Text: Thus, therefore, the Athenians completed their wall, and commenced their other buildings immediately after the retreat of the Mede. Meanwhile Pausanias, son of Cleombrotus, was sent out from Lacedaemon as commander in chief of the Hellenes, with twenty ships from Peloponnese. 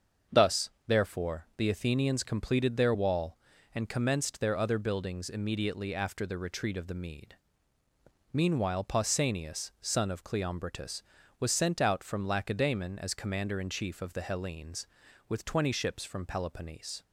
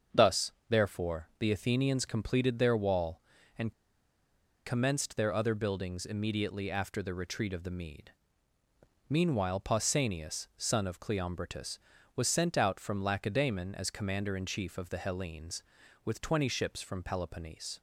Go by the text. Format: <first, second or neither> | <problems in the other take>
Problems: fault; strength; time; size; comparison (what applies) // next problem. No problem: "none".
first | starts louder than the rest; until 1.4 s; 6.5 dB; also in the first // pauses between "and" and "commenced"; noticeable; at 3.7 s; 0.93 s long